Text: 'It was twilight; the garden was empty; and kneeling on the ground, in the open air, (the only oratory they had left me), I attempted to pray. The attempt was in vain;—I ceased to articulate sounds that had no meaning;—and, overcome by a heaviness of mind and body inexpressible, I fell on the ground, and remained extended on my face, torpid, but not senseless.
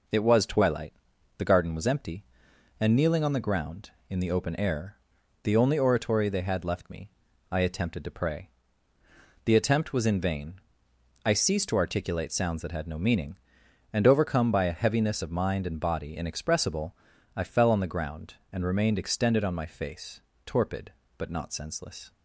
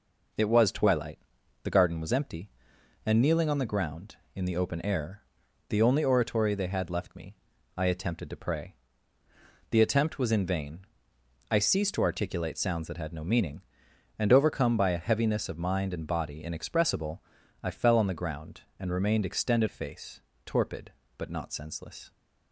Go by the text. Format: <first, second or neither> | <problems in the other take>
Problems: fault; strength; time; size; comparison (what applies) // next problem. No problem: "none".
first | skips "on my"; at 19.6 s